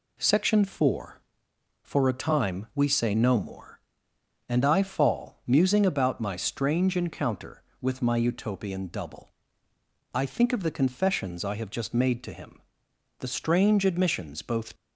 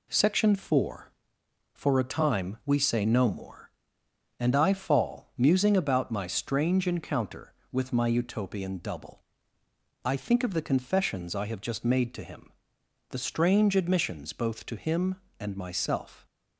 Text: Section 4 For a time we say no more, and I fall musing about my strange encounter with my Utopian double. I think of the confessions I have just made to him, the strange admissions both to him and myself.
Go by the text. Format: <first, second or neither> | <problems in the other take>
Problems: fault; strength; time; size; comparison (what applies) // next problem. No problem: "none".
second | stops before "to him and myself"; at 14.7 s